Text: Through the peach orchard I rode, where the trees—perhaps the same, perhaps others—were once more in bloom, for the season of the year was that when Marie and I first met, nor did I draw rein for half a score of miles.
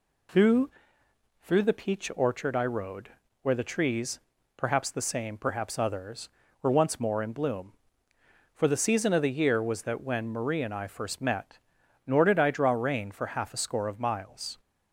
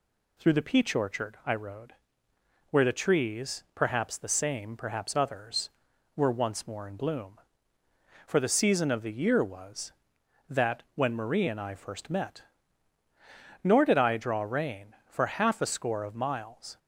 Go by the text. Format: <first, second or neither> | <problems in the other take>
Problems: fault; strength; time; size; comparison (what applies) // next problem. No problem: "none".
second | says "Through" twice; at 1.4 s